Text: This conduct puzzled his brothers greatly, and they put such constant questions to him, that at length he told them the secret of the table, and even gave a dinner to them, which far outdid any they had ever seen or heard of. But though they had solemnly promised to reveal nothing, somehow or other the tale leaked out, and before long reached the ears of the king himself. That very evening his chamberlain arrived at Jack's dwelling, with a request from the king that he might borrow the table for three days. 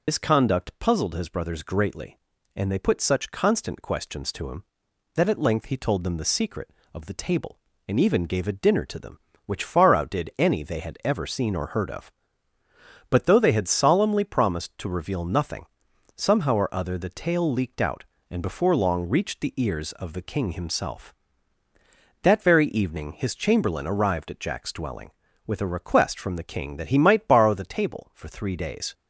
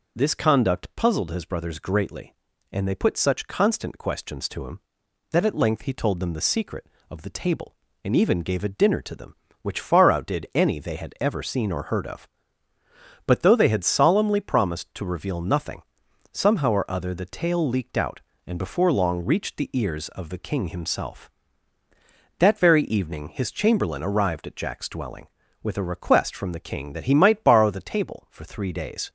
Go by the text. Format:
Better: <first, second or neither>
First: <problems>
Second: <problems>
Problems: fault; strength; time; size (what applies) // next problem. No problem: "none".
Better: second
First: loses the start of "This"; at 0.0 s; 85 ms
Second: none